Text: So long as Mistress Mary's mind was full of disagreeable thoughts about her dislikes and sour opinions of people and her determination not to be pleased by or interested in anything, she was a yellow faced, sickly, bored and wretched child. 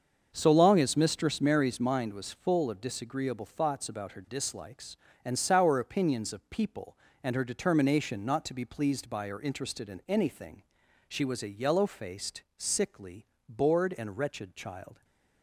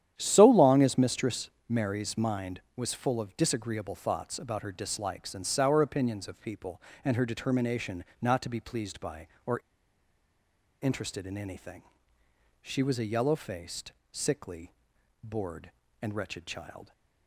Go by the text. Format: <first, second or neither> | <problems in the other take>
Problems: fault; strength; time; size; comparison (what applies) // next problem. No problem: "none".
first | starts louder than the rest; strong; until 1.2 s; 10.5 dB; also in the first // pauses between "Mistress" and "Mary's"; slight; at 1.4 s; 0.18 s long // pauses between "determination" and "not"; slight; at 8.0 s; 0.20 s long // pauses between "or" and "interested"; at 9.5 s; 1.2 s long